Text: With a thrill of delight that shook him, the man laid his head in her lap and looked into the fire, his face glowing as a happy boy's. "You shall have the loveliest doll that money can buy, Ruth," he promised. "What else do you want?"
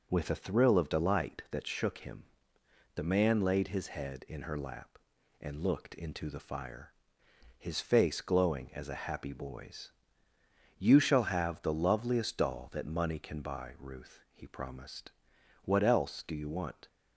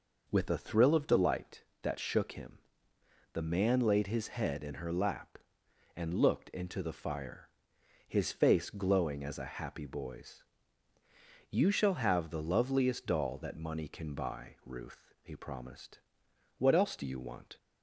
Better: neither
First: none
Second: none

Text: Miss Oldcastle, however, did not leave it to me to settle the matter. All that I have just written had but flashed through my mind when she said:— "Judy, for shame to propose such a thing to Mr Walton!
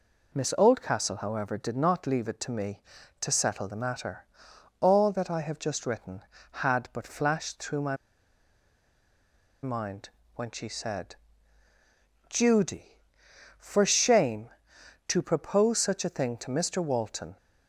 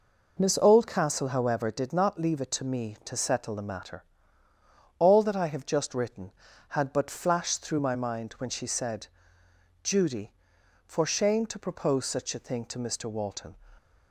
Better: second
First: pauses between "my" and "mind"; strong; at 7.9 s; 1.6 s long // pauses between "mind" and "when"; slight; at 10.0 s; 0.26 s long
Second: none

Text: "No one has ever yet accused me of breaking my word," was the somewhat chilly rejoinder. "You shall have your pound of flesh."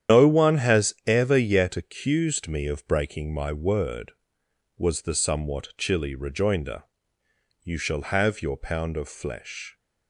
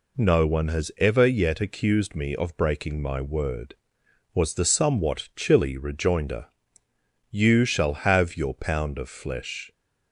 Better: second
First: loses the start of "No"; at 0.0 s; 145 ms // starts louder than the rest; strong; until 1.2 s; 9.5 dB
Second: none

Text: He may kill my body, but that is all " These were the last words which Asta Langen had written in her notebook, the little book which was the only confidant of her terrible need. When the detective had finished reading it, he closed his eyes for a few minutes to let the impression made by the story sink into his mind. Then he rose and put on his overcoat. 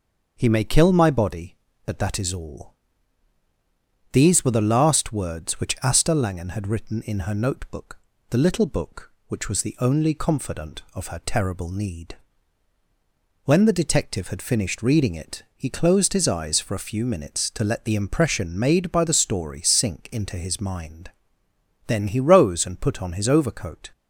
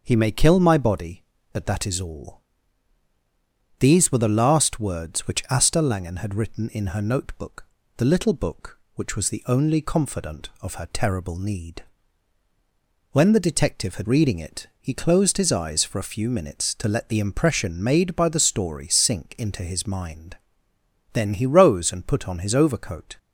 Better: first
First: none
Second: skips "finished"; at 14.0 s

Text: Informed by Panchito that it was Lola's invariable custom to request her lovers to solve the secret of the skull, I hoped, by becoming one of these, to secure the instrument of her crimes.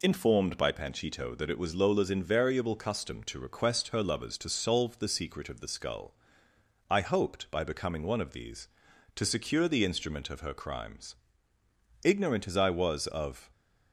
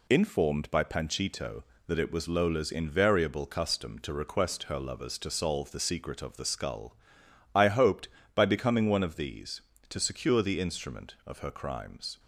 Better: second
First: goes on to say "Ignorant as I was of"; from 12.0 s on; 1.4 s long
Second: none

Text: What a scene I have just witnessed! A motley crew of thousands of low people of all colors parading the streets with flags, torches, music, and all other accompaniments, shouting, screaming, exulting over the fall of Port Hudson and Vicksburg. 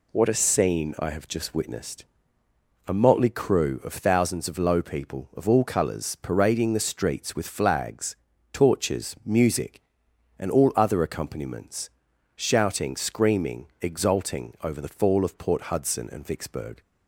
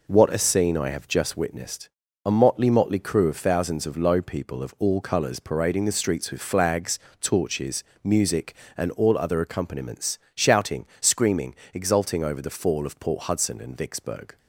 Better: first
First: none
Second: says "motley" twice; at 2.6 s

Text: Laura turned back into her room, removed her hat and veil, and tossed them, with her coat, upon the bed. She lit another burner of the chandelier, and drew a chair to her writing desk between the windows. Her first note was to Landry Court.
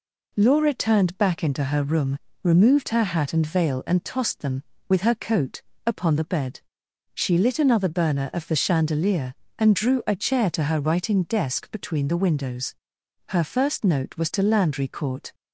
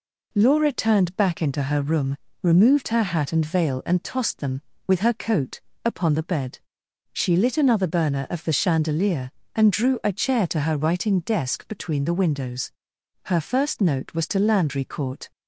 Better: neither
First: none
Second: none

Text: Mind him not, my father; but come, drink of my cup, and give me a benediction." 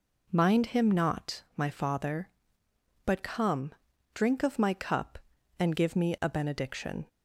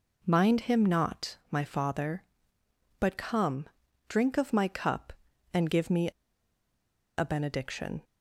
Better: first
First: none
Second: pauses between "me" and "a"; at 6.0 s; 1.0 s long

